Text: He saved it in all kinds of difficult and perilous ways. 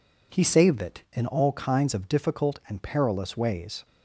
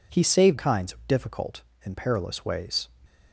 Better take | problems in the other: first | skips "it in all"; at 0.5 s

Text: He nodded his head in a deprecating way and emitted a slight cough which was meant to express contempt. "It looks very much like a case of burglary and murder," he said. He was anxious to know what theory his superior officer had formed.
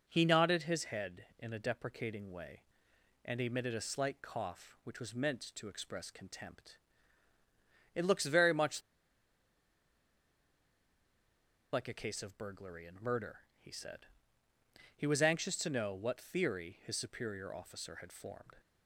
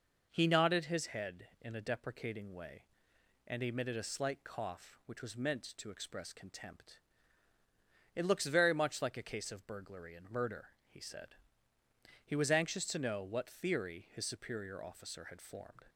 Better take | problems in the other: second | pauses between "much" and "like"; strong; at 8.7 s; 2.9 s long

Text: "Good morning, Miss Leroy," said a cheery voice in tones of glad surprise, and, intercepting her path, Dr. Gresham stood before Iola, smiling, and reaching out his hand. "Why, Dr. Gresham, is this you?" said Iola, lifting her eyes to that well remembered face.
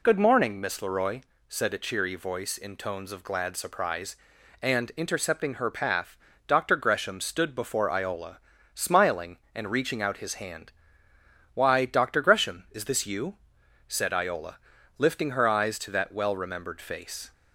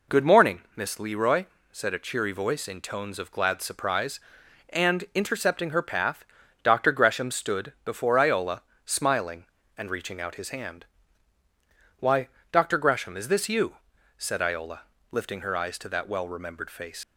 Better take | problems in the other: first | leaves "face" unfinished; at 17.0 s; 85 ms

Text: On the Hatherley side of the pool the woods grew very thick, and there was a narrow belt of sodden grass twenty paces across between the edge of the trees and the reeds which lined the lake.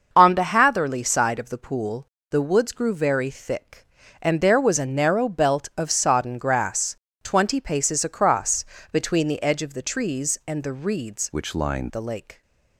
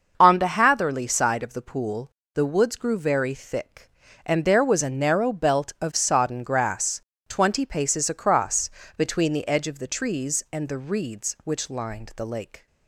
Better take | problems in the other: second | starts louder than the rest; until 1.1 s; 6.5 dB; also in the second // pauses between "pool" and "the"; slight; at 2.0 s; 0.26 s long; slight in the second // pauses between "grass" and "twenty"; slight; at 6.9 s; 0.26 s long; slight in the second // pauses between "across" and "between"; slight; at 8.6 s; 0.26 s long; slight in the second // changes voice from "which" to "lined"; from 11.3 to 11.9 s; 0.6 s long

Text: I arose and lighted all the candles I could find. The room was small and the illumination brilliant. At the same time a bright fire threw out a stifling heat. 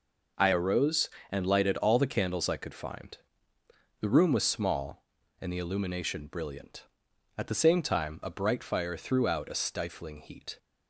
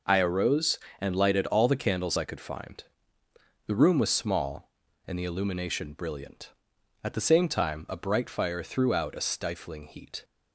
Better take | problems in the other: neither | none

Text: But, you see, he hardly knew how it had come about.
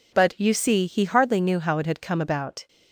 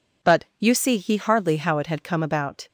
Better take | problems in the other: first | skips "knew"; at 1.5 s

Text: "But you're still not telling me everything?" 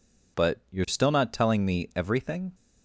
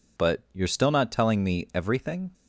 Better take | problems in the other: neither | none

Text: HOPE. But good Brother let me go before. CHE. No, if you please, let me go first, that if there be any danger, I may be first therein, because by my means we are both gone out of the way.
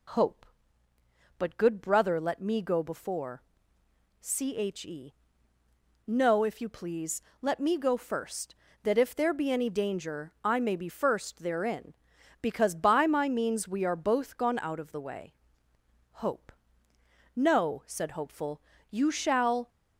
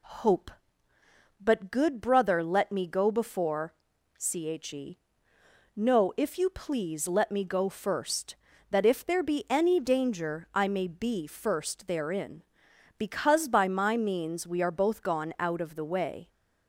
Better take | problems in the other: second | goes on to say "HOPE No said Hopeful you shall"; strong; from 16.1 s on; 3.5 s long

